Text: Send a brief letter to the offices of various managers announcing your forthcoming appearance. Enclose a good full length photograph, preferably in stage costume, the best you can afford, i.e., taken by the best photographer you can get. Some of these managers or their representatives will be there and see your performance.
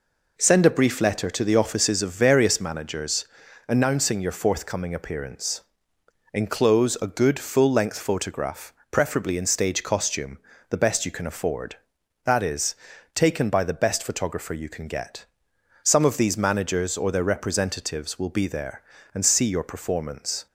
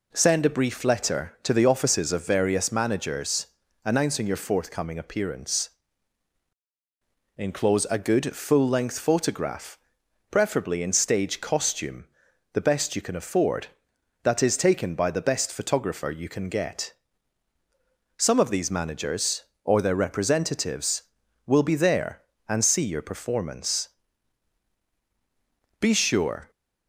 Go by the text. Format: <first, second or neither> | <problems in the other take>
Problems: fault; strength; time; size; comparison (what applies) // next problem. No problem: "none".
first | pauses between "managers" and "announcing"; at 3.4 s; 0.38 s long; also in the first // goes on to say "Be sure"; noticeable; from 25.7 s on; 0.72 s long